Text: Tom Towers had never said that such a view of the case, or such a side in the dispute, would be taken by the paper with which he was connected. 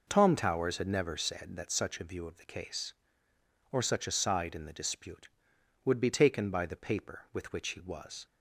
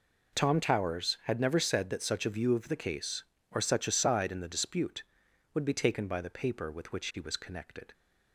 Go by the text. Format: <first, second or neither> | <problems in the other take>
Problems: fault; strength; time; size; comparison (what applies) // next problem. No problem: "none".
second | stops before "connected"; at 8.2 s